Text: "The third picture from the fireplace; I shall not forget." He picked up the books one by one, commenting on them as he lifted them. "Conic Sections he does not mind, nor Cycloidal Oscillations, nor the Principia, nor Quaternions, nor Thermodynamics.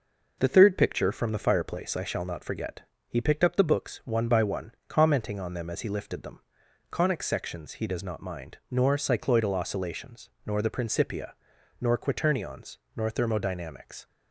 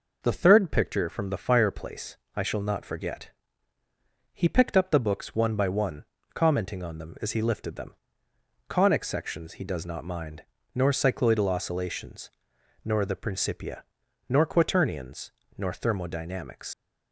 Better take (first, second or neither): first